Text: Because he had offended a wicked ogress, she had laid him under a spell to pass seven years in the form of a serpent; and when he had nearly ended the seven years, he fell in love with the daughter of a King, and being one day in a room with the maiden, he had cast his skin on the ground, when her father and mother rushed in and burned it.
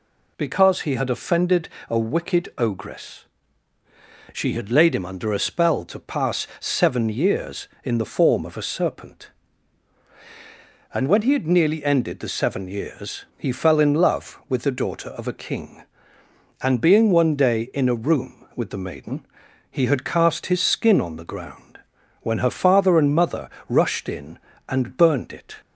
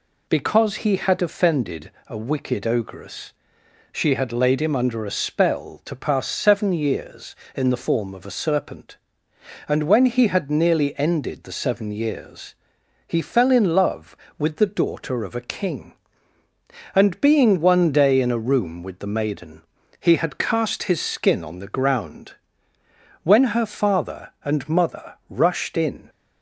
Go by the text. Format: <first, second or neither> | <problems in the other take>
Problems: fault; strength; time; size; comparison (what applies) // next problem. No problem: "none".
first | pauses between "offended" and "a"; slight; at 1.8 s; 0.18 s long; slight in the first // pauses between "mother" and "rushed"; slight; at 25.1 s; 0.16 s long; slight in the first // stops before "and burned it"; at 26.0 s